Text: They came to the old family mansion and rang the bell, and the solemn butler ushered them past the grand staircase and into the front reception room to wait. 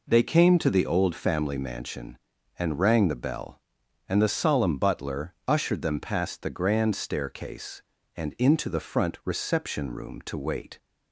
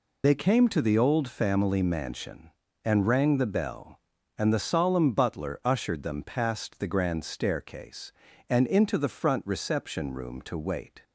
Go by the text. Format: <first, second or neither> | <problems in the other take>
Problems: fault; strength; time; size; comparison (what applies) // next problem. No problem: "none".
first | loses the start of "They"; at 0.2 s; 70 ms